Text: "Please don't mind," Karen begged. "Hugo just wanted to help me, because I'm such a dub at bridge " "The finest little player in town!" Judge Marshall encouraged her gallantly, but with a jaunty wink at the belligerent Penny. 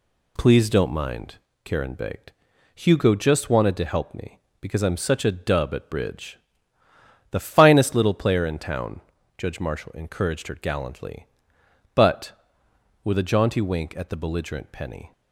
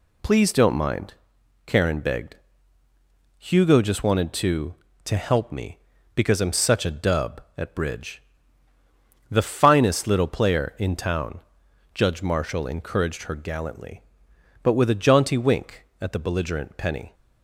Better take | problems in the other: first | says "to" twice; at 5.0 s

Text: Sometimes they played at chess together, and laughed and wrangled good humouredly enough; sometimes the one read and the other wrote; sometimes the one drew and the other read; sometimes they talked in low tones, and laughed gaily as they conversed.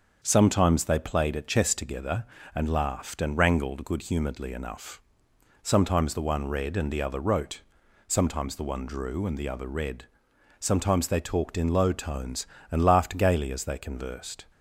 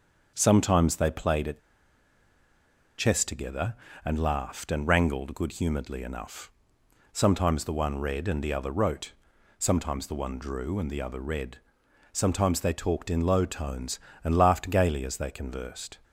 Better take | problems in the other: first | starts louder than the rest; until 1.3 s; 6.5 dB; also in the first // pauses between "at" and "chess"; strong; at 1.5 s; 1.3 s long

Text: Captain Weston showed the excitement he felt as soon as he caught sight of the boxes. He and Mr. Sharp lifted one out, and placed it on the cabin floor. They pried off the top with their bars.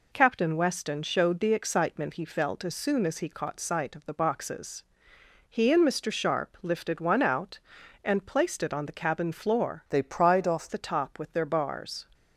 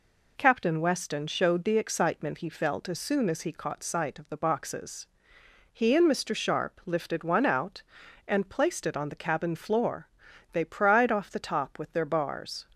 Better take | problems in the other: second | changes voice from "They" to "off"; from 9.8 to 10.6 s; 0.8 s long

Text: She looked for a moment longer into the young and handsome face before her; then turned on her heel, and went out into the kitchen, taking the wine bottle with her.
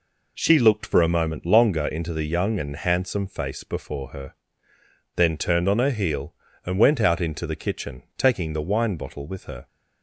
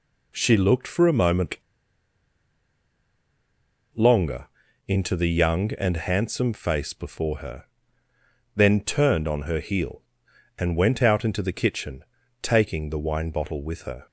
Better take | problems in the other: first | pauses between "moment" and "longer"; strong; at 1.5 s; 2.3 s long // pauses between "longer" and "into"; at 4.4 s; 0.40 s long

